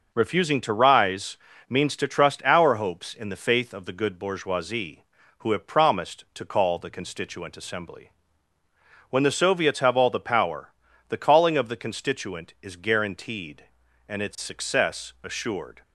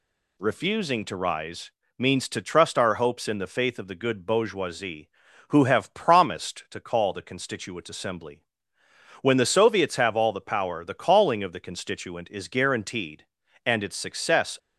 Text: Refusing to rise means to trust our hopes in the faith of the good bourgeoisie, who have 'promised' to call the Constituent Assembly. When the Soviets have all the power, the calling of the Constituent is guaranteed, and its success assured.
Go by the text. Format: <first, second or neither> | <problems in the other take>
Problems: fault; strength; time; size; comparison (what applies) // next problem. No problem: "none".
first | pauses between "rise" and "means"; slight; at 1.7 s; 0.26 s long; slight in the first // stops before "assured"; at 14.5 s